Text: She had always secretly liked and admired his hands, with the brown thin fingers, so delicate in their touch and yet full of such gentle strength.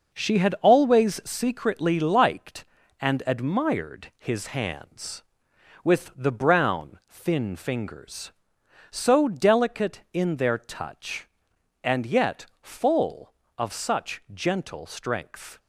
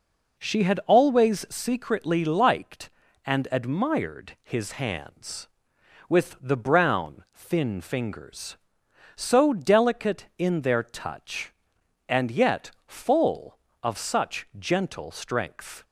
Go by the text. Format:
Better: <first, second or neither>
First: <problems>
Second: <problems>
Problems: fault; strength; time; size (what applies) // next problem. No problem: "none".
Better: second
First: gets quieter; strong; throughout; 7 dB // pauses between "yet" and "full"; slight; at 12.4 s; 0.16 s long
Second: pauses between "yet" and "full"; slight; at 12.7 s; 0.16 s long